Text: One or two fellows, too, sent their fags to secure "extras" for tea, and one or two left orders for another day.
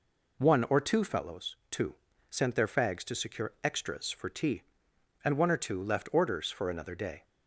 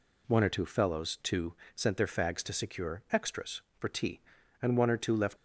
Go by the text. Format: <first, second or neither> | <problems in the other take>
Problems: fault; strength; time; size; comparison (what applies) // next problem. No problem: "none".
first | stops before "orders for another day"; at 5.3 s